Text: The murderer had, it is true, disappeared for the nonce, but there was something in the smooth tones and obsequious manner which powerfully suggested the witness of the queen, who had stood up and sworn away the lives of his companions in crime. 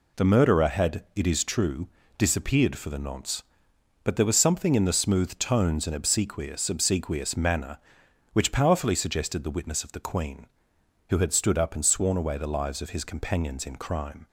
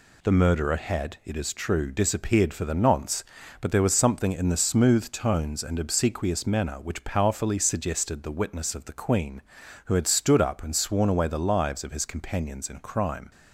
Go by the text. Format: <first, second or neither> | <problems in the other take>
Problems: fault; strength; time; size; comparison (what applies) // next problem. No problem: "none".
second | says "obsequious" twice; at 6.6 s